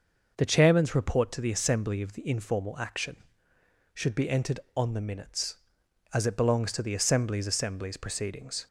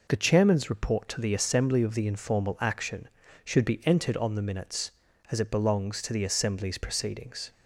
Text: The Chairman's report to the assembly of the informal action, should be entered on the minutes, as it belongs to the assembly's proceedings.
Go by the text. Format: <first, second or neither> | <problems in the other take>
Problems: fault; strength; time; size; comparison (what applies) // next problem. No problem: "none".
second | starts louder than the rest; noticeable; until 1.3 s; 6 dB // says "assembly's" twice; at 7.4 s